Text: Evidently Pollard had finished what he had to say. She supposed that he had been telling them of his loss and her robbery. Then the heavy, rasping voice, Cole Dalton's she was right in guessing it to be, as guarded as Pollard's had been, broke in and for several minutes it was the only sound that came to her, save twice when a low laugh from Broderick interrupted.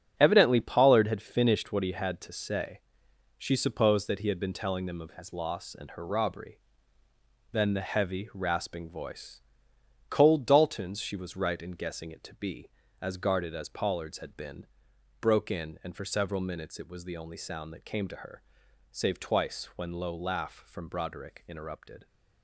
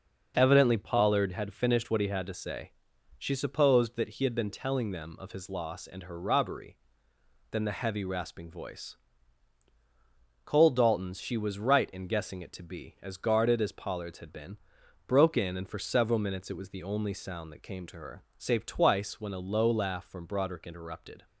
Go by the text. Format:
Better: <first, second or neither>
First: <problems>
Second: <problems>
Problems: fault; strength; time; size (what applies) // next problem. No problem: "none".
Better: second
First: starts louder than the rest; strong; until 1.2 s; 8.5 dB // skips "a"; at 19.9 s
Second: none